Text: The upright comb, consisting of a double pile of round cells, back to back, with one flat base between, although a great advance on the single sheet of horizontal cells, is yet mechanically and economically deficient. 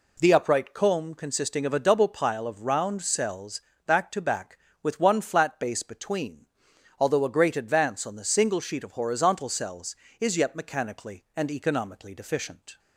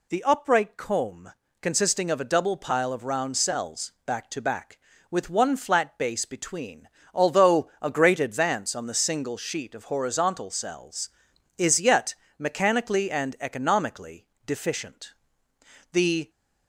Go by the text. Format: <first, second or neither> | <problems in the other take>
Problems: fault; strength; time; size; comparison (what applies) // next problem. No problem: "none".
first | pauses between "yet" and "mechanically"; slight; at 12.1 s; 0.24 s long // pauses between "economically" and "deficient"; slight; at 14.2 s; 0.20 s long // goes on to say "The"; slight; from 15.9 s on; 0.38 s long